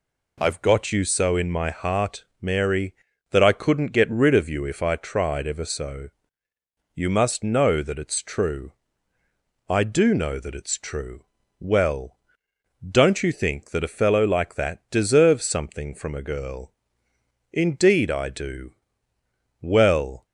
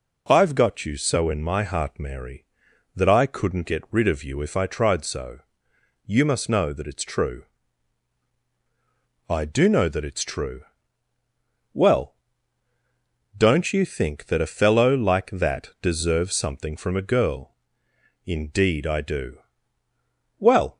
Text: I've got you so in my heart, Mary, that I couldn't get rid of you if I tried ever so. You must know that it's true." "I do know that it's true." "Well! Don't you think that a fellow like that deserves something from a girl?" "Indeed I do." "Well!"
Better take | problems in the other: first | skips "ever"; at 5.0 s

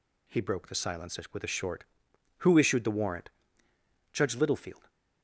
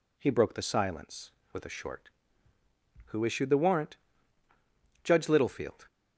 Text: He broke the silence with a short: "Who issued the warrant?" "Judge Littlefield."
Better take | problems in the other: neither | none

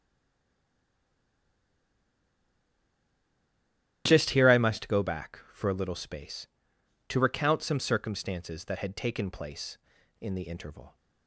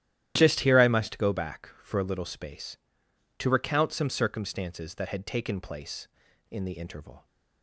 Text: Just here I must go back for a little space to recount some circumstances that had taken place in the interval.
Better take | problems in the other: second | stays silent before the first word; strong; until 4.0 s; 4.0 s long // starts louder than the rest; strong; until 5.0 s; 12.5 dB; strong in the second

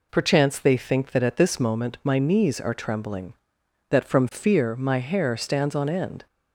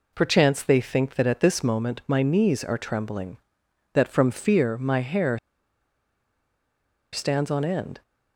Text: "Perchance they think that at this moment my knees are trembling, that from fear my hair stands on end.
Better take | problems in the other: first | pauses between "hair" and "stands"; strong; at 5.3 s; 1.7 s long

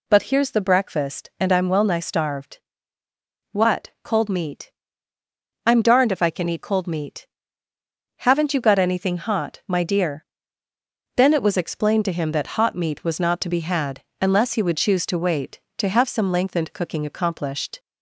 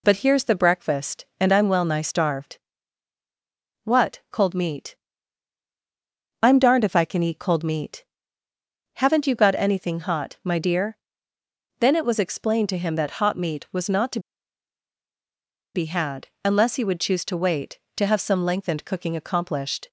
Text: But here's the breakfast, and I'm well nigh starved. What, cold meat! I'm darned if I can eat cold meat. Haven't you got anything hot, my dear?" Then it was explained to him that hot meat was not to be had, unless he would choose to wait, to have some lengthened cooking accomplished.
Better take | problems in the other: first | pauses between "to" and "be"; strong; at 14.1 s; 1.5 s long

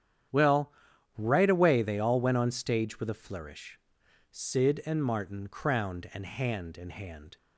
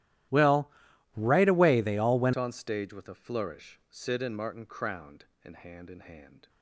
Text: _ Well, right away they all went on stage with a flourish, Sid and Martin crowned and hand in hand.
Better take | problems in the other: first | starts louder than the rest; strong; until 1.7 s; 14.5 dB; strong in the first // changes voice at "on"; from 2.3 s on; 4.1 s long

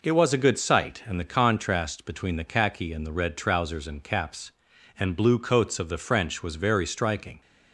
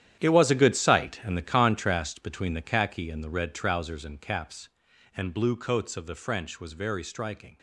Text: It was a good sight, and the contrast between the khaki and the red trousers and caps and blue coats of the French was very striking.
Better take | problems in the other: first | gets quieter; strong; throughout; 12.5 dB

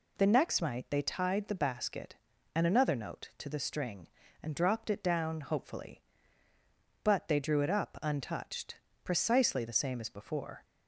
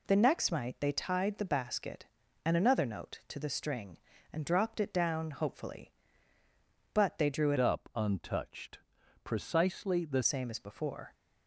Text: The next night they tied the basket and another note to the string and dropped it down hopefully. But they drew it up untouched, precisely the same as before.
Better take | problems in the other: first | changes voice from "up" to "the"; from 7.5 to 10.2 s; 2.7 s long

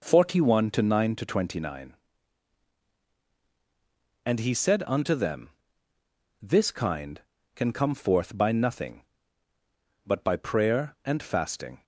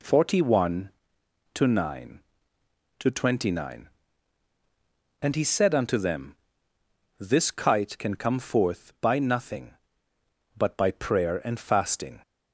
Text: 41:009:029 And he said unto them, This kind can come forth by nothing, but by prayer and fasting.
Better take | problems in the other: first | says "kite" for "kind"; at 7.5 s

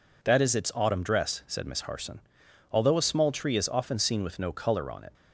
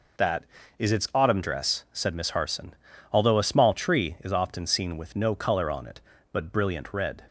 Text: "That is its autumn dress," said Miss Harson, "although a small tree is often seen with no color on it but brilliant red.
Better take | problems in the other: second | stops before "but brilliant red"; at 5.1 s

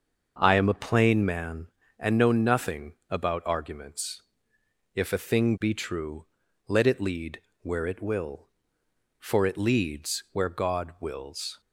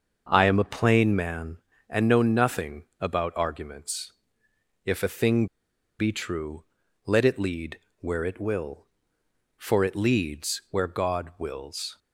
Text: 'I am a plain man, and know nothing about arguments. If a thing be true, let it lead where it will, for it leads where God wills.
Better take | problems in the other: first | starts louder than the rest; until 1.3 s; 6.5 dB; also in the first // pauses between "nothing" and "about"; slight; at 2.8 s; 0.16 s long; slight in the first // pauses between "thing" and "be"; noticeable; at 5.4 s; 0.53 s long // pauses between "lead" and "where"; slight; at 7.8 s; 0.18 s long; slight in the first

